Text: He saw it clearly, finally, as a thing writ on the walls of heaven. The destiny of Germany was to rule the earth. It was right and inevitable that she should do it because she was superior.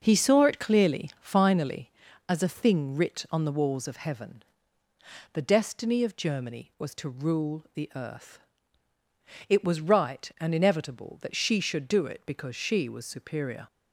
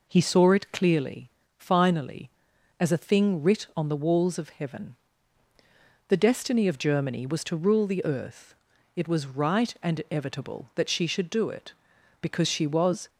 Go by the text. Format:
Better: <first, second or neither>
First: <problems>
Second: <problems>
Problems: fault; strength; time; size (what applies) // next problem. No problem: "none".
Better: first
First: none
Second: stops before "superior"; at 13.0 s